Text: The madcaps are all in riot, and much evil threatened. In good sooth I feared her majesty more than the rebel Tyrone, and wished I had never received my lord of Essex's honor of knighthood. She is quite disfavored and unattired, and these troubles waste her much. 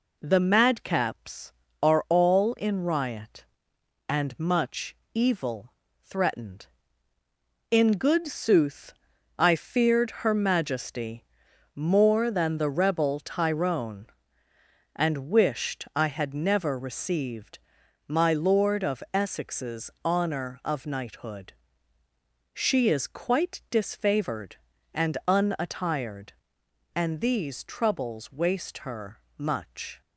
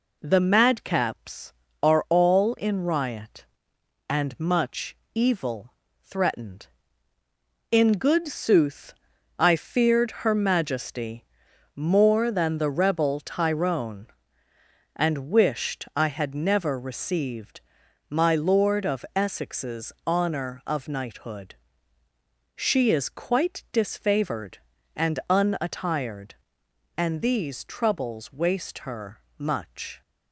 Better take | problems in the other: neither | pauses between "much" and "evil"; slight; the same in both // pauses between "evil" and "threatened"; slight; the same in both // pauses between "sooth" and "I"; the same in both // pauses between "majesty" and "more"; noticeable; the same in both // pauses between "received" and "my"; noticeable; the same in both // pauses between "her" and "much"; slight; the same in both

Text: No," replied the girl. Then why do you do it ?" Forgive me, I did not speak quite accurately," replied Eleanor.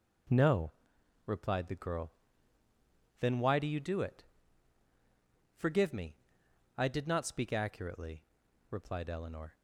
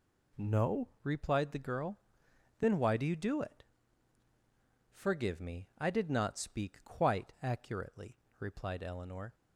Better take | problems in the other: second | skips "quite"; at 7.5 s

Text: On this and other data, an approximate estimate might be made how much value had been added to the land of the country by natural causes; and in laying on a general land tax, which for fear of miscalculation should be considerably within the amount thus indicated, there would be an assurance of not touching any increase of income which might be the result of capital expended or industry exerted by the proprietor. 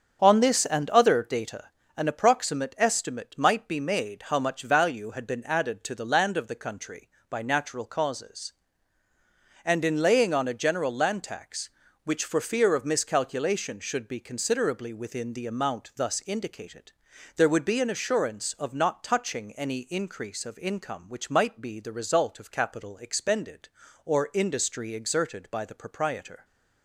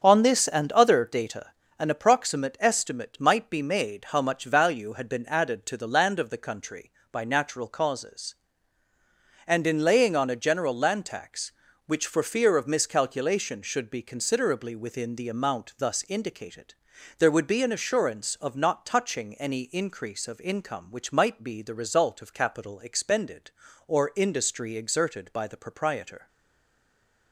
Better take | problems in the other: first | starts louder than the rest; strong; until 1.0 s; 7.5 dB; strong in the first // stays silent after the last word; from 26.2 s on; 1.1 s long

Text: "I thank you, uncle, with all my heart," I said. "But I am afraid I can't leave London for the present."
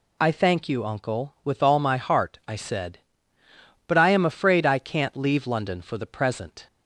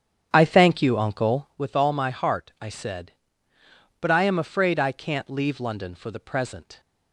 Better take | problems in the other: first | starts louder than the rest; strong; until 1.5 s; 9 dB

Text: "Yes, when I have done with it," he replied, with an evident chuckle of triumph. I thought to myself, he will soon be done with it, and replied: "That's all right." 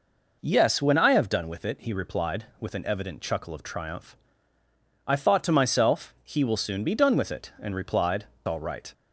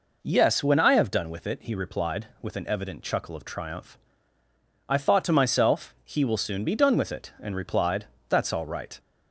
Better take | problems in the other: second | skips "That's"; at 8.3 s

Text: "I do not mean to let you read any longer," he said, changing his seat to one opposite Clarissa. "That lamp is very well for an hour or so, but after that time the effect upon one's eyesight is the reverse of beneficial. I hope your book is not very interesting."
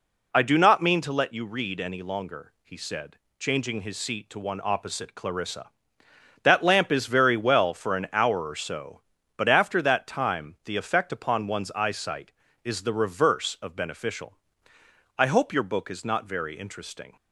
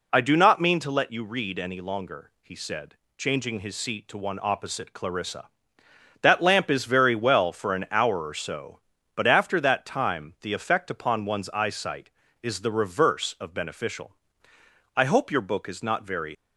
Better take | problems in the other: first | stops before "interesting"; at 16.3 s

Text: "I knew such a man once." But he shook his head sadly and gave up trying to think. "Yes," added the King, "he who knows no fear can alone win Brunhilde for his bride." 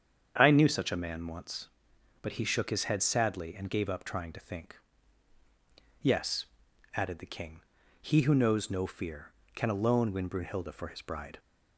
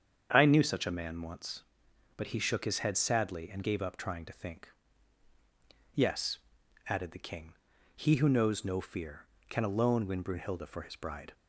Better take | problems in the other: neither | starts louder than the rest; strong; the same in both

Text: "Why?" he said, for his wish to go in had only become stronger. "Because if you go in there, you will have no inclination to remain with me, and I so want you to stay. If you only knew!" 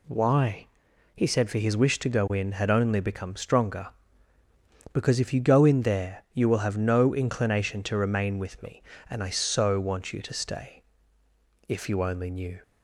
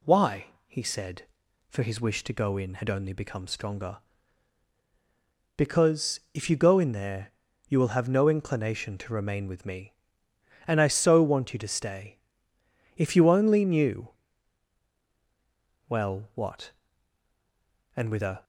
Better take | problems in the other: first | pauses between "Because" and "if"; slight; at 6.1 s; 0.16 s long // goes on to say "Well what And with a"; strong; from 15.8 s on; 2.5 s long

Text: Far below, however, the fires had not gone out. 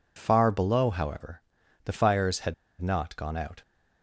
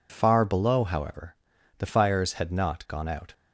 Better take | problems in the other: second | pauses between "had" and "not"; slight; at 2.5 s; 0.27 s long

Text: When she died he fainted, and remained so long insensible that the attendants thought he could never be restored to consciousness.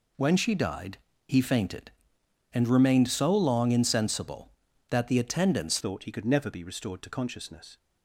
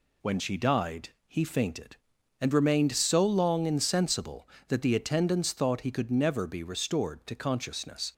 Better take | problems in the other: second | pauses between "died" and "he"; slight; at 0.9 s; 0.30 s long; slight in the second // changes voice at "thought"; from 5.8 s on; 1.9 s long

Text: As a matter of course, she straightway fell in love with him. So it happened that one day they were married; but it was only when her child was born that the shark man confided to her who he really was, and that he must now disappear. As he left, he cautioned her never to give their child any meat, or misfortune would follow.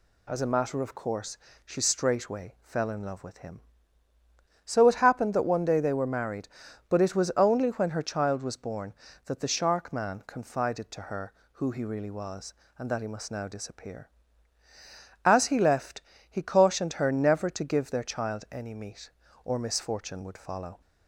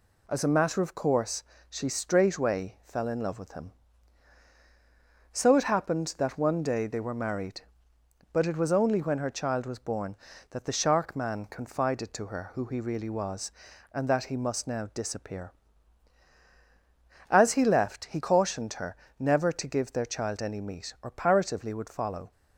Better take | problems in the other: first | pauses between "her" and "never"; slight; at 18.9 s; 0.24 s long // says "paratively" for "misfortune"; at 21.0 s

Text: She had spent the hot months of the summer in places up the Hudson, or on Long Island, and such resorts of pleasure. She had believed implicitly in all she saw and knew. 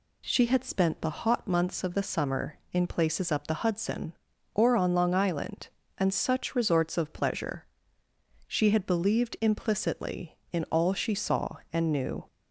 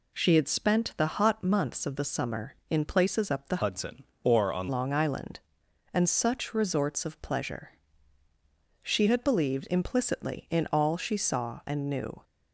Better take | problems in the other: first | changes voice from "Hudson" to "on"; from 3.6 to 4.6 s; 1.0 s long

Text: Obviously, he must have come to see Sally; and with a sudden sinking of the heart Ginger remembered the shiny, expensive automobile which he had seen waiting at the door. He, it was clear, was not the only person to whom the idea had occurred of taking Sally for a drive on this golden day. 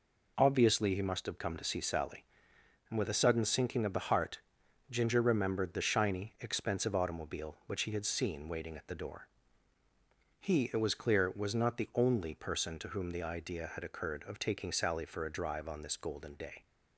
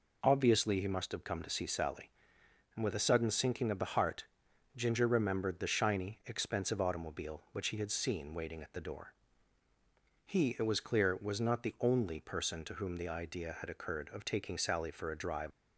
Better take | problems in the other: first | pauses between "heart" and "Ginger"; noticeable; at 4.2 s; 0.50 s long; noticeable in the first // stops before "on this golden day"; at 15.5 s

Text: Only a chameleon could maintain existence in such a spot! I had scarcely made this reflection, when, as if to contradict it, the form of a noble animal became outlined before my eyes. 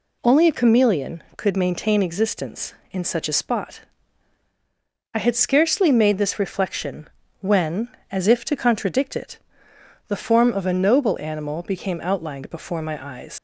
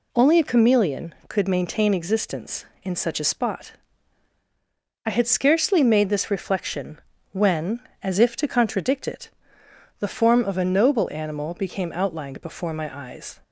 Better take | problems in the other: second | leaves "eyes" unfinished; at 13.3 s; 125 ms

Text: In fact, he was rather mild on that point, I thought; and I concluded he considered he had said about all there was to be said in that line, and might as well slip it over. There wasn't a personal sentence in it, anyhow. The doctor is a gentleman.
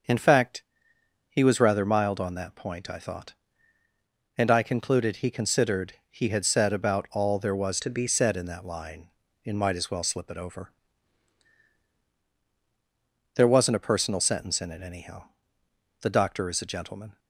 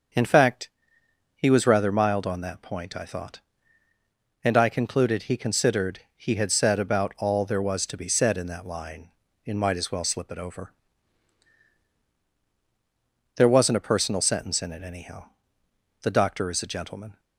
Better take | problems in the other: second | starts louder than the rest; until 1.7 s; 6.5 dB; also in the second // pauses between "considered" and "he"; slight; at 5.9 s; 0.16 s long; slight in the second // changes voice from "to" to "be"; from 7.8 to 8.0 s; 0.2 s long

